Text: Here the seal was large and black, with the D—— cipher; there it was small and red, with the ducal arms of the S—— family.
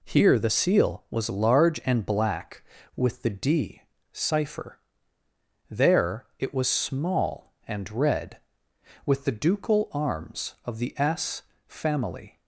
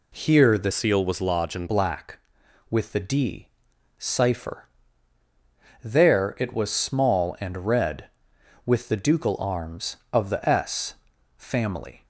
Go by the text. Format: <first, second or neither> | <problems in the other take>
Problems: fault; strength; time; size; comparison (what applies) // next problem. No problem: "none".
first | changes voice from "seal" to "and"; from 0.7 to 1.6 s; 0.9 s long